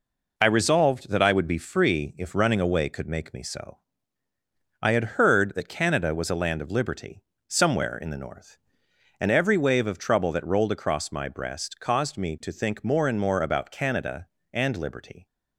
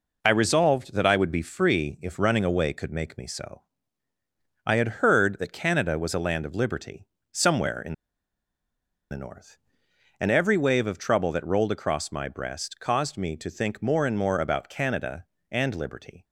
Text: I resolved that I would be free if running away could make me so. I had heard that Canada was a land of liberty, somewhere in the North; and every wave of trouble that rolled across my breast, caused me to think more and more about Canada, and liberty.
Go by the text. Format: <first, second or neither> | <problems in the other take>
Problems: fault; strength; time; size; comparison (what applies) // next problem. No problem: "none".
first | pauses between "in" and "the"; at 7.9 s; 1.1 s long